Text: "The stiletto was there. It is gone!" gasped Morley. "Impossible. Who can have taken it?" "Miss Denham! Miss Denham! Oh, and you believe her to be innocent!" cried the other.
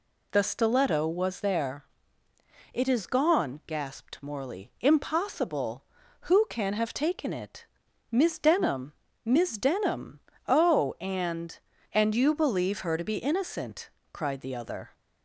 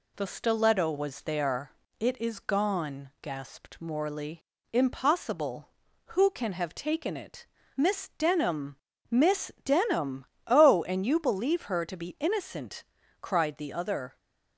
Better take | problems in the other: second | says "and" twice; at 11.9 s

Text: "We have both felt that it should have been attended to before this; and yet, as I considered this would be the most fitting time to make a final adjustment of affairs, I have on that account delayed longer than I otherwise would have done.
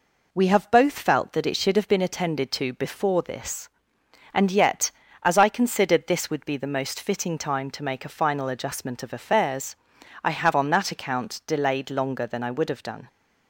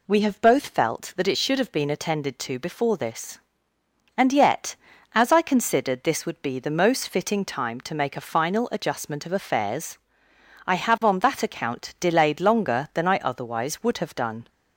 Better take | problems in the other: second | skips "otherwise"; at 12.5 s

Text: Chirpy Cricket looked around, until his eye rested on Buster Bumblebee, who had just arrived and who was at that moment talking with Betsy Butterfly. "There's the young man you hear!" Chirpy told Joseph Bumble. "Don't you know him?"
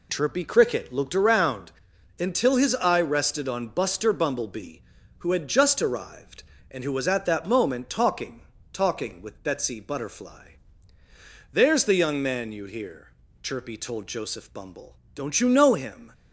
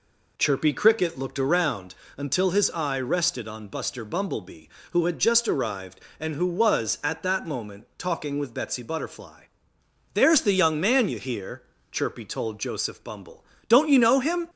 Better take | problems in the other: second | says "talking" twice; at 8.7 s

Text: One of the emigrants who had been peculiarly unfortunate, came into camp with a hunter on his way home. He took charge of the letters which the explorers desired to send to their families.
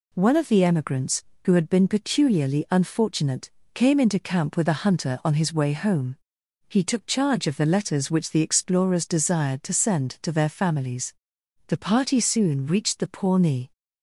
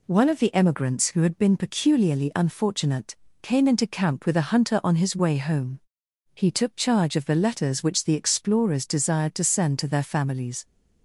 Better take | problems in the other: second | goes on to say "The party soon reached the Pawnee"; strong; from 11.6 s on; 2.0 s long

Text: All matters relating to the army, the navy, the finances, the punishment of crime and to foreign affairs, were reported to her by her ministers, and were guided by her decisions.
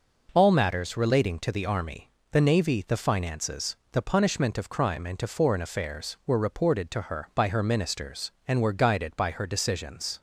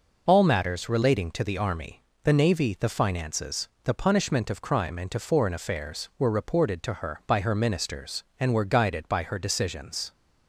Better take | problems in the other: first | loses the start of "All"; at 0.2 s; 50 ms

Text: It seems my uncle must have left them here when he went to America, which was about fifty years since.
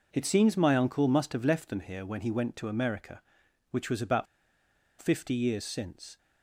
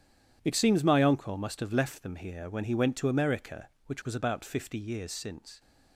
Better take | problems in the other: second | pauses between "about" and "fifty"; noticeable; at 4.2 s; 0.75 s long

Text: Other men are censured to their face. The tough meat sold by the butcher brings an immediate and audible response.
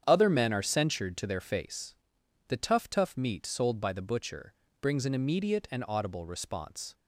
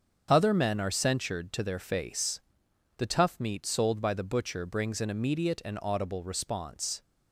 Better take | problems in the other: second | starts louder than the rest; strong; until 1.0 s; 8.5 dB; strong in the second // says "tough" twice; at 2.9 s // pauses between "butcher" and "brings"; slight; at 4.5 s; 0.30 s long

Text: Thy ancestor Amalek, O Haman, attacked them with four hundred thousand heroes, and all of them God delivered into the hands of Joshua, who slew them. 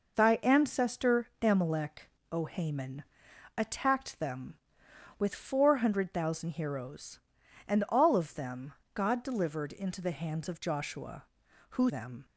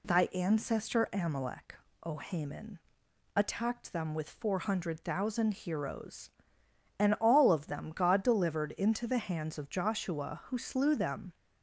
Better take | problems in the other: second | pauses between "them" and "God"; slight; at 8.7 s; 0.22 s long // skips "slew"; at 11.8 s

